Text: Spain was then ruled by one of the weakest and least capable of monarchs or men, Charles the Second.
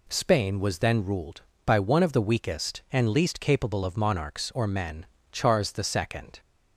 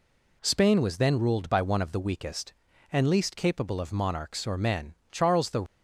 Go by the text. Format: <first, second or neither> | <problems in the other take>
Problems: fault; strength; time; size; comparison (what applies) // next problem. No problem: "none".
first | stops before "Second"; at 5.6 s